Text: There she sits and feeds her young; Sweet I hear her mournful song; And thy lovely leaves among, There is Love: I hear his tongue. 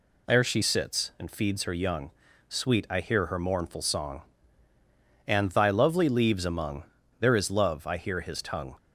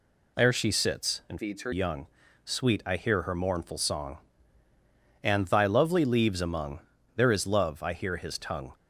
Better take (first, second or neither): first